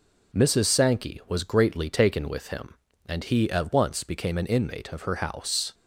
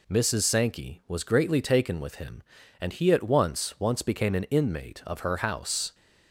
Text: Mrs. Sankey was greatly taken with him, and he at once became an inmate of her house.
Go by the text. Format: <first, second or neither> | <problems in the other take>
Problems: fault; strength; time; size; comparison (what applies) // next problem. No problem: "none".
first | says "once" twice; at 3.8 s